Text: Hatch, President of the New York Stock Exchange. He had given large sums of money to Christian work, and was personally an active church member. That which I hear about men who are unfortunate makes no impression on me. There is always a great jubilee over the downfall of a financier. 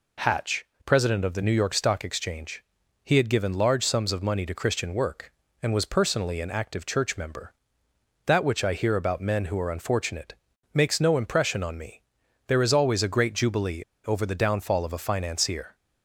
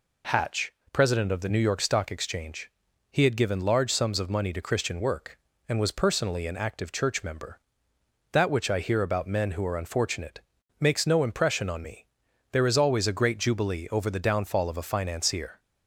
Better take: second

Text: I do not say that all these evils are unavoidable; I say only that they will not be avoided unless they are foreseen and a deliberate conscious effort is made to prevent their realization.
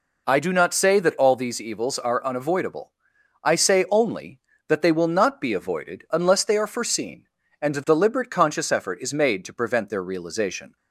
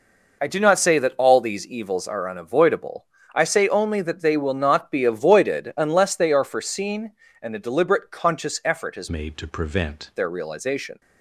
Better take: first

